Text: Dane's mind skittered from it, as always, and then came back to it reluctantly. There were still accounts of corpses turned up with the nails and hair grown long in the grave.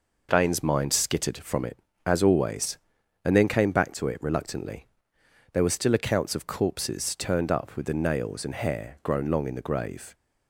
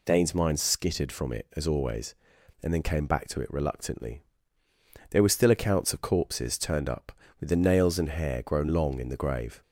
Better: neither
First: none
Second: none

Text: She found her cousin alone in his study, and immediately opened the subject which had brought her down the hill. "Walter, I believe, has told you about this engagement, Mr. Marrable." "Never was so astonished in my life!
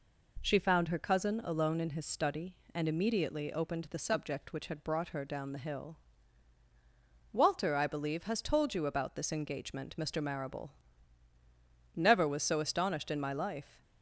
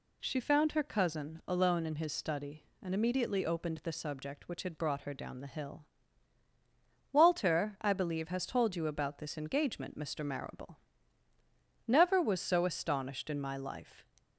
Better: neither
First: none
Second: none

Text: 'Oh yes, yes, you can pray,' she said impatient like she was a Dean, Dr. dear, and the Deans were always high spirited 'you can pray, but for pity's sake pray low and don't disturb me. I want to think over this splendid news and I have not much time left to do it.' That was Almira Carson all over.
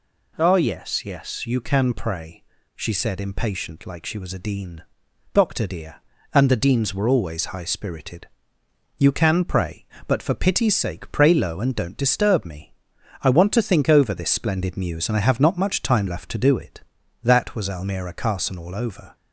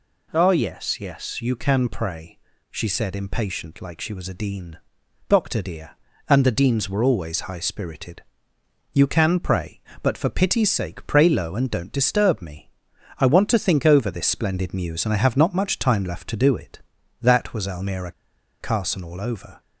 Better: first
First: pauses between "spirited" and "you"; noticeable; at 8.2 s; 0.70 s long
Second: pauses between "spirited" and "you"; noticeable; at 8.2 s; 0.70 s long // pauses between "Almira" and "Carson"; noticeable; at 18.1 s; 0.49 s long

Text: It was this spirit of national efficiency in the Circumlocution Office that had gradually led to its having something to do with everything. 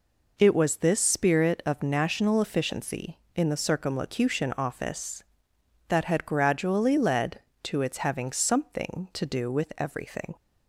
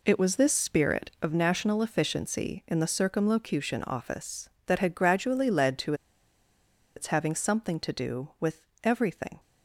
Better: first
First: none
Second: pauses between "to" and "its"; at 5.9 s; 1.0 s long // pauses between "with" and "everything"; slight; at 8.6 s; 0.22 s long

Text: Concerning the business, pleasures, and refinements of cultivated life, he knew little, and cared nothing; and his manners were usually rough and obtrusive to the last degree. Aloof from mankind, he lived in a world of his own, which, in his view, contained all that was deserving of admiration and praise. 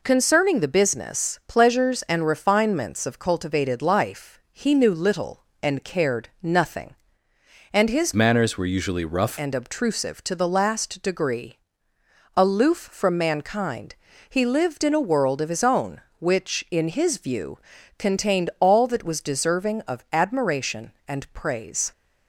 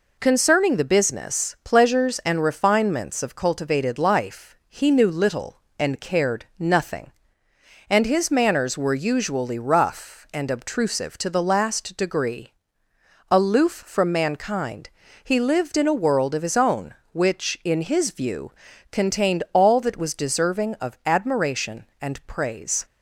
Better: second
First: changes voice from "manners" to "rough"; from 8.1 to 9.3 s; 1.2 s long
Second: none

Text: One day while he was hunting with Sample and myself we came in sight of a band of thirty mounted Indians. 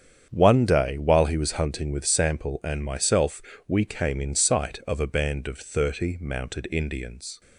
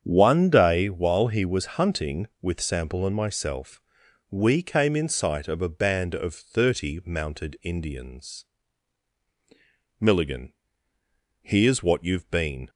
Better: first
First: starts louder than the rest; strong; until 1.3 s; 8.5 dB // pauses between "myself" and "we"; slight; at 3.4 s; 0.28 s long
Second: starts louder than the rest; strong; until 1.0 s; 7.5 dB // pauses between "myself" and "we"; noticeable; at 3.7 s; 0.50 s long // goes on to say "Milligan here's what you've been"; strong; from 10.0 s on; 2.6 s long

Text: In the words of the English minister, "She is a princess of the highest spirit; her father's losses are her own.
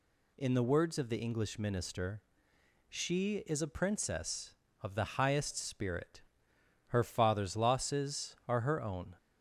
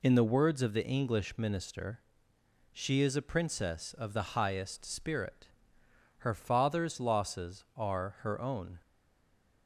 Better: first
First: none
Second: stays silent after the last word; slight; from 8.8 s on; 0.8 s long

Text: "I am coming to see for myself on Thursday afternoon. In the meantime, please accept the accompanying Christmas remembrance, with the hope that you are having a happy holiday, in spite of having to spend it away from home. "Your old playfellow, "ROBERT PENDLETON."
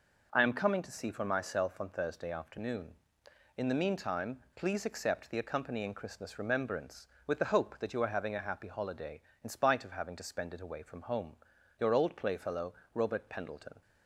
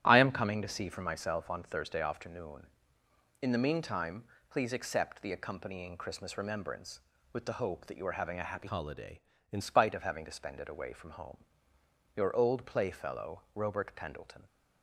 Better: first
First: none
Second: starts louder than the rest; strong; until 1.0 s; 11.5 dB // changes voice from "holiday" to "in"; from 8.6 to 9.6 s; 1.0 s long

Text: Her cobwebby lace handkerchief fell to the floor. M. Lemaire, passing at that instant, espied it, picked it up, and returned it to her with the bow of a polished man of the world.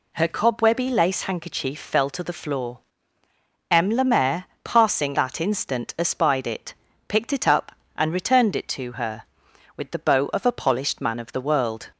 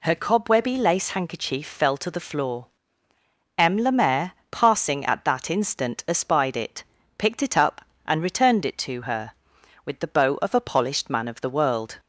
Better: second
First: skips "at"; at 5.1 s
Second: none

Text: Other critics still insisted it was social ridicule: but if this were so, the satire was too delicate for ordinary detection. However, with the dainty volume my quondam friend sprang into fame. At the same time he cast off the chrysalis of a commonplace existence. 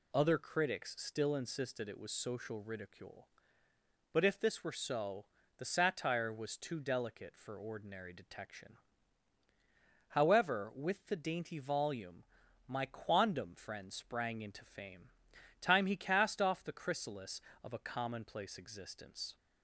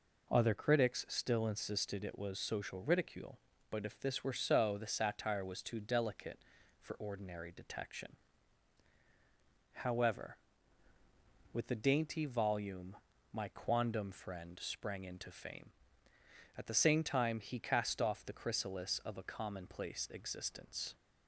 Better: second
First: pauses between "volume" and "my"; at 12.2 s; 0.42 s long // skips "At the same"; at 15.3 s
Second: pauses between "volume" and "my"; slight; at 12.9 s; 0.36 s long

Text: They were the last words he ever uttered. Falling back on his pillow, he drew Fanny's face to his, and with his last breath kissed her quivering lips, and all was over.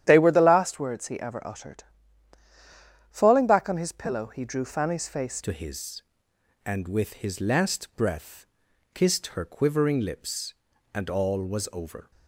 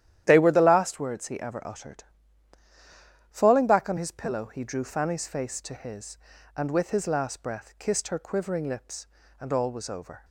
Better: second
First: starts louder than the rest; strong; until 1.0 s; 10.5 dB // changes voice at "to"; from 5.4 s on; 6.7 s long // pauses between "breath" and "kissed"; noticeable; at 8.4 s; 0.48 s long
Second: starts louder than the rest; strong; until 1.2 s; 11.5 dB

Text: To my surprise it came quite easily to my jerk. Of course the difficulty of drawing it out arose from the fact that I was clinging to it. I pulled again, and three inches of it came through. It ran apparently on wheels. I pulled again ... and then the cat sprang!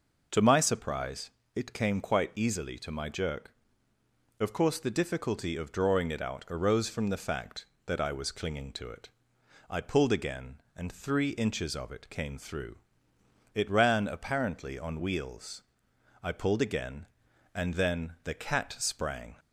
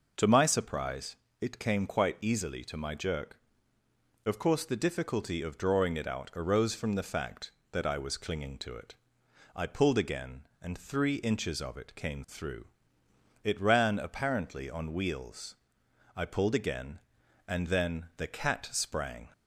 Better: neither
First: pauses between "surprise" and "it"; slight; at 1.2 s; 0.24 s long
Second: pauses between "surprise" and "it"; slight; at 1.1 s; 0.24 s long

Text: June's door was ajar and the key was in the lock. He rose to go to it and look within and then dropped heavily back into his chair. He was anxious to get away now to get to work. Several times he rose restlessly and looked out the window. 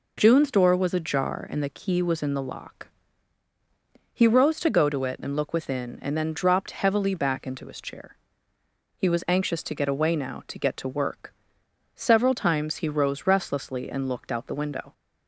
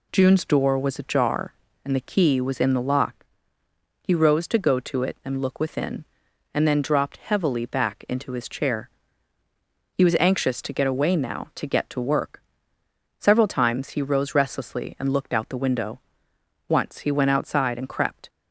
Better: first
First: none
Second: goes on to say "Once he went outside and crept"; from 16.6 s on; 1.6 s long

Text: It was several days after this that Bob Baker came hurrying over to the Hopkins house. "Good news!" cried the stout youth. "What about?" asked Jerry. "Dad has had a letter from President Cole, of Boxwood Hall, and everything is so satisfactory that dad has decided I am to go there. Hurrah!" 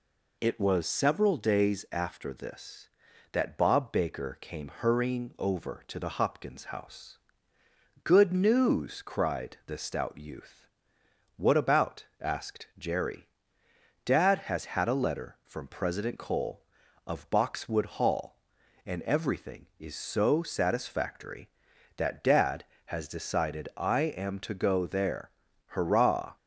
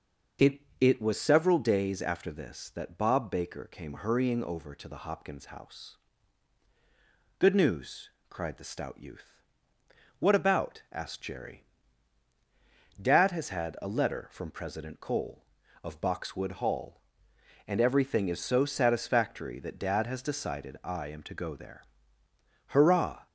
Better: first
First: none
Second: starts louder than the rest; noticeable; until 1.5 s; 6 dB // says "It" twice; at 0.8 s

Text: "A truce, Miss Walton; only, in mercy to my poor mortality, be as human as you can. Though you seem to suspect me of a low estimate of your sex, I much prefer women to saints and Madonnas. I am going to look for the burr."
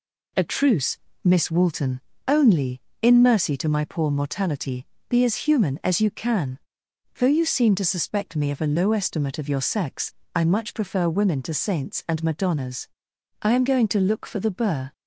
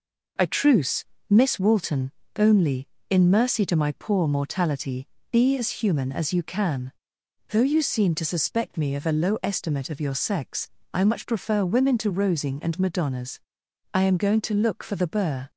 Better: first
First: none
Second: says "rosing" for "saints"; at 12.0 s

